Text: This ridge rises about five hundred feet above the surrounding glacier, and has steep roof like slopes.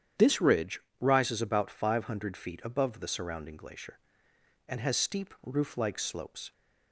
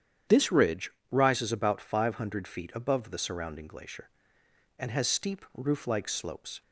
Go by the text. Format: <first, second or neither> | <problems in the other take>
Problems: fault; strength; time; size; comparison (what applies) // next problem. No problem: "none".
neither | starts louder than the rest; strong; the same in both // pauses between "ridge" and "rises"; slight; the same in both